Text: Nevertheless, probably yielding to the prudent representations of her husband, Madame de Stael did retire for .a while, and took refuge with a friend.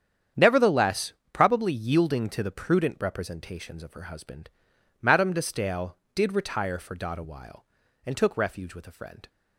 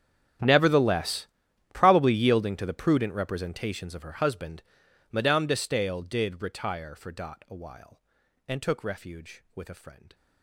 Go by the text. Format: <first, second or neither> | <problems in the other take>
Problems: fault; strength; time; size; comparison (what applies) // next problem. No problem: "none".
first | gets quieter; strong; throughout; 22.5 dB // starts louder than the rest; strong; until 1.8 s; 9.5 dB; strong in the first